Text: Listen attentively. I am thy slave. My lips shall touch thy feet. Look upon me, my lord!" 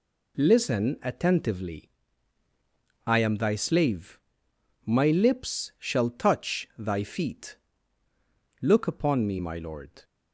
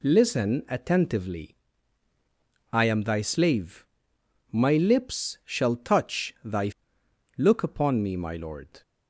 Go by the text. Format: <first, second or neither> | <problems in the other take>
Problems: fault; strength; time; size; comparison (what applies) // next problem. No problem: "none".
first | skips "feet"; at 7.0 s